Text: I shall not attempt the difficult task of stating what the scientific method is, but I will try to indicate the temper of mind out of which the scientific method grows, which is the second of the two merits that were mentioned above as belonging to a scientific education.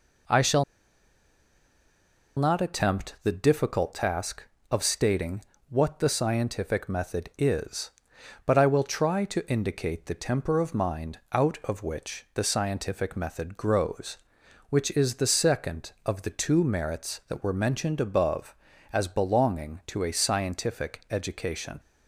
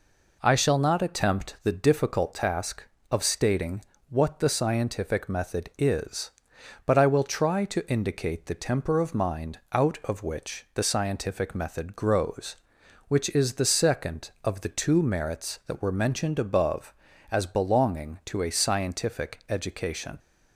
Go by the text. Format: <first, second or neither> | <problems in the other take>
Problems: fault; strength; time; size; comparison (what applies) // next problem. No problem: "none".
second | pauses between "shall" and "not"; strong; at 0.6 s; 1.7 s long // pauses between "stating" and "what"; slight; at 5.4 s; 0.26 s long; slight in the second